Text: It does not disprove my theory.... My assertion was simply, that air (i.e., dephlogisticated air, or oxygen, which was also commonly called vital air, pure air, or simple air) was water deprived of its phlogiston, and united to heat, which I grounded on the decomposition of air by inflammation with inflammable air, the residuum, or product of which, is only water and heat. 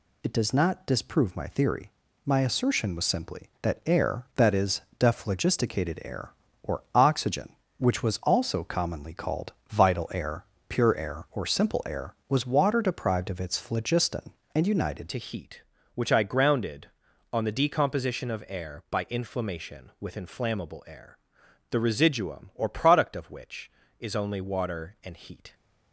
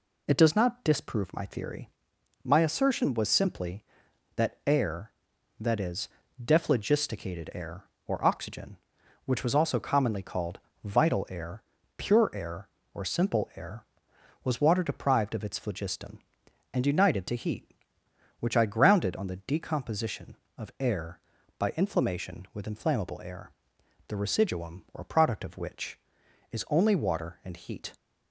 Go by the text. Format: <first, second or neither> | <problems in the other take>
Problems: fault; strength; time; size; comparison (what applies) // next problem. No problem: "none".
second | pauses between "called" and "vital"; slight; at 9.5 s; 0.16 s long; slight in the second // changes voice at "to"; from 15.0 s on; 10.5 s long